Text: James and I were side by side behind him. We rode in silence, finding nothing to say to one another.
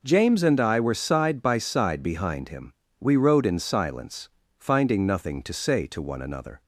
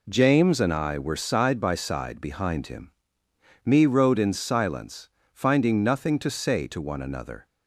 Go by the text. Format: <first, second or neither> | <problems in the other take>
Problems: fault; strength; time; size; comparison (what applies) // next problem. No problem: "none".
first | says "Me" for "We"; at 3.6 s